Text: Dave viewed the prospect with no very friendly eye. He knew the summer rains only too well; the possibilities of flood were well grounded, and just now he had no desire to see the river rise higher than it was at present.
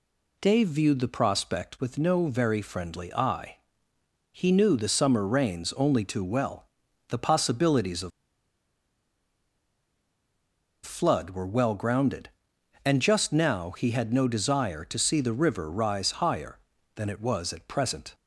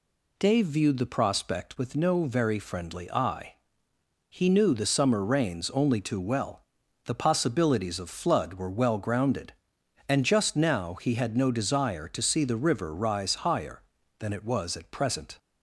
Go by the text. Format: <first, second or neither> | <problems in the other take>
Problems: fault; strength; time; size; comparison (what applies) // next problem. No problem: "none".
second | pauses between "of" and "flood"; strong; at 8.1 s; 2.7 s long